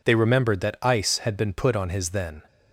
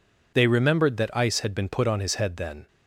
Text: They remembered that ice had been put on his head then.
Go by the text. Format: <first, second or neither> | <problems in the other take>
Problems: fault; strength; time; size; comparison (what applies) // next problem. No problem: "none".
second | skips "head"; at 2.1 s